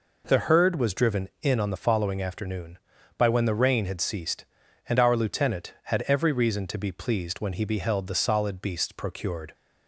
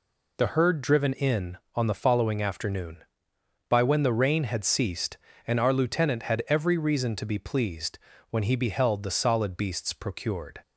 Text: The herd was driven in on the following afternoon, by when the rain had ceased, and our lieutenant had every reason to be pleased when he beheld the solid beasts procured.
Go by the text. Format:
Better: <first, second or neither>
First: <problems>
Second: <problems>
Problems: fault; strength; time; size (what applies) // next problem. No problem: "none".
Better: first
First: none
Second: skips "was"; at 0.8 s // pauses between "pleased" and "when"; slight; at 7.9 s; 0.34 s long